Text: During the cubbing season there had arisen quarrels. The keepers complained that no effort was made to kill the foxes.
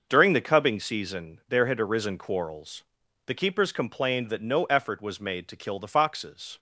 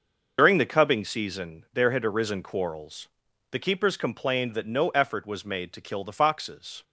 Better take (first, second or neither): first